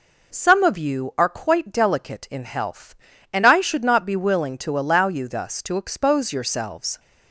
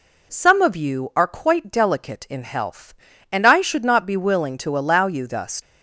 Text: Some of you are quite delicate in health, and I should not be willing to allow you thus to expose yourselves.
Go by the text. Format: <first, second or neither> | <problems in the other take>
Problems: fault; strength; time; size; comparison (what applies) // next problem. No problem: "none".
first | stops before "to expose yourselves"; at 5.5 s